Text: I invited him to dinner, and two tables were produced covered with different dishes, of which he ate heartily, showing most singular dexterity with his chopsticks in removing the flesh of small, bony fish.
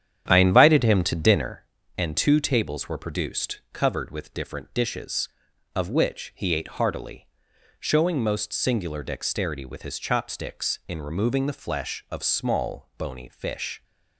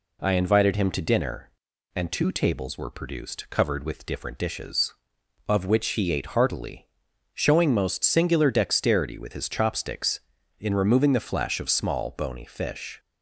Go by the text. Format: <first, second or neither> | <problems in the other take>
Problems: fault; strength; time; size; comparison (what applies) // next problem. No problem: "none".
second | starts louder than the rest; strong; until 1.6 s; 9.5 dB